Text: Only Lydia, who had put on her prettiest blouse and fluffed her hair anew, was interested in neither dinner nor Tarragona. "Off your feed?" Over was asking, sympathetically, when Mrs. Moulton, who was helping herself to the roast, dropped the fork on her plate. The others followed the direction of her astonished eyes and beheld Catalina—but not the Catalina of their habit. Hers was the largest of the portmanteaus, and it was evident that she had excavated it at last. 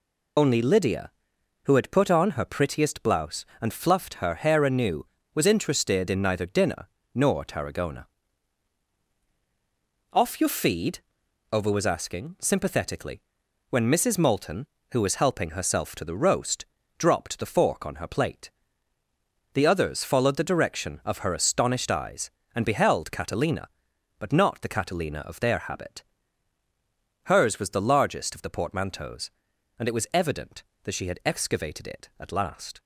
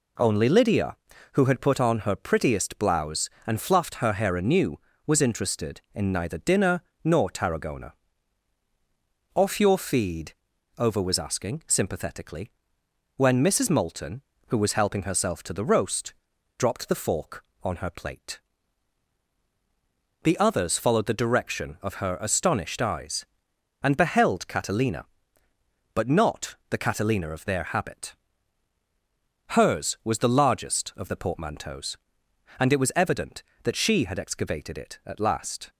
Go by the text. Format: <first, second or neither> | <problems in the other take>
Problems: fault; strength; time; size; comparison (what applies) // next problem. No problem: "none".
second | loses the start of "Only"; at 0.3 s; 55 ms // pauses between "dinner" and "nor"; slight; at 6.8 s; 0.26 s long; slight in the second